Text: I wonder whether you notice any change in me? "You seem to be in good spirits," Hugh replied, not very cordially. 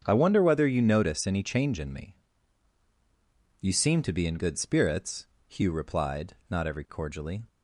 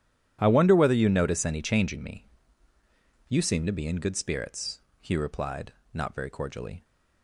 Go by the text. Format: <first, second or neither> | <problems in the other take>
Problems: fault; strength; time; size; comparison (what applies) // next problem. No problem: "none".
second | starts louder than the rest; strong; until 1.0 s; 7.5 dB // says "every" for "very"; at 6.6 s